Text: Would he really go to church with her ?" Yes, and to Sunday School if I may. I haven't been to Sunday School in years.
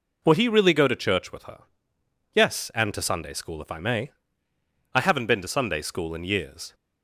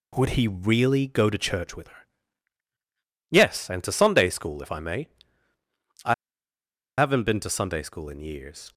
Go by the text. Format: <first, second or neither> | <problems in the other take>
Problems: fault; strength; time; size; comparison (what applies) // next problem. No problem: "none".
first | pauses between "I" and "haven't"; noticeable; at 6.1 s; 0.84 s long